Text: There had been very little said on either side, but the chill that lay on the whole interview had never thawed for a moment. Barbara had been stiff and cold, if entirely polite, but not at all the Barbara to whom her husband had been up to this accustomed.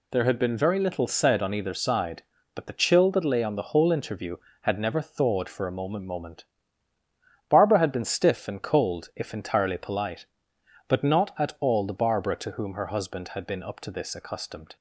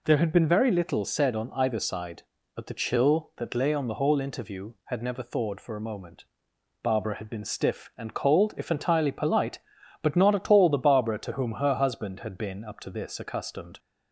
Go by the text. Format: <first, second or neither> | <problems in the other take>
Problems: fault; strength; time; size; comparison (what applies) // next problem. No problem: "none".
second | says "moment" twice; at 6.0 s